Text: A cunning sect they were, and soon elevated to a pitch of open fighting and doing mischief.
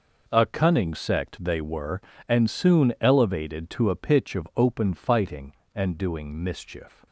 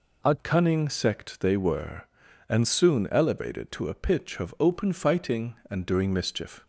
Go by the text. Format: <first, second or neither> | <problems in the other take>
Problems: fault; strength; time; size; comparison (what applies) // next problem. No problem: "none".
first | changes voice at "cunning"; from 0.3 s on; 6.3 s long